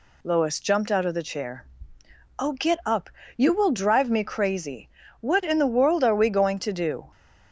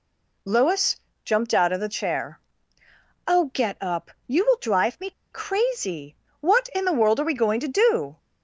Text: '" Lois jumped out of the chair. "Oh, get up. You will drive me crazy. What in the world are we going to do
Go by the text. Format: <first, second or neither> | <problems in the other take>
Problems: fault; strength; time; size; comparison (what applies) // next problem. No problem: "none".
first | pauses between "Lois" and "jumped"; slight; at 0.9 s; 0.26 s long // pauses between "me" and "crazy"; slight; at 5.1 s; 0.20 s long